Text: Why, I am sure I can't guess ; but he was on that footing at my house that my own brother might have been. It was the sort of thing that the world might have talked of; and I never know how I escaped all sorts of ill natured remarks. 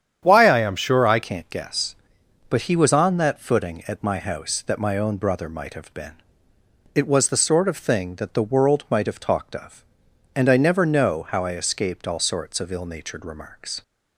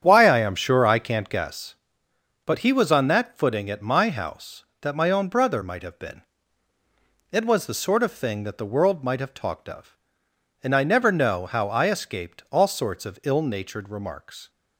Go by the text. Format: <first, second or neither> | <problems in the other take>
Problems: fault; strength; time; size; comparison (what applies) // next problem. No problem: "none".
second | starts louder than the rest; strong; until 1.2 s; 8.5 dB; strong in the second // changes voice at "can't"; from 1.2 s on; 12.6 s long